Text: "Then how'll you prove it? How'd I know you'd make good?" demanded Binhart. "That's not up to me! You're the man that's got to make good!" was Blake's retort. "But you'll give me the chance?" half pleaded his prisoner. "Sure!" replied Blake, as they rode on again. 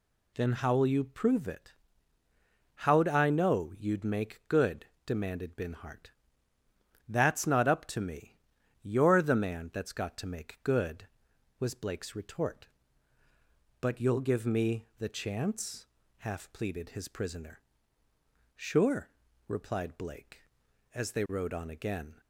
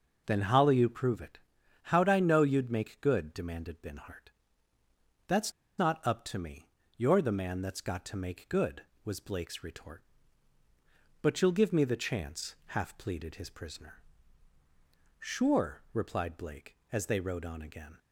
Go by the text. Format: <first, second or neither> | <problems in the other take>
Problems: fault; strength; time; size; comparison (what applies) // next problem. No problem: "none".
first | pauses between "That's" and "not"; slight; at 5.5 s; 0.26 s long